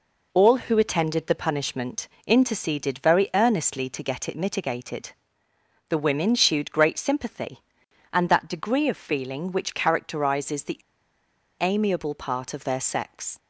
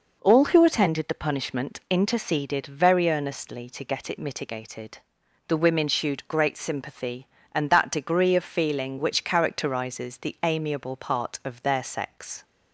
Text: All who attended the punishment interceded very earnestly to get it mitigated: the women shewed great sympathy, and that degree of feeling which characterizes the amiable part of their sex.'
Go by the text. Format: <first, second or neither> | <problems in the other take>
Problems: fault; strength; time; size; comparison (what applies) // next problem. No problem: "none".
second | pauses between "punishment" and "interceded"; slight; at 2.0 s; 0.18 s long // pauses between "the" and "amiable"; noticeable; at 10.8 s; 0.79 s long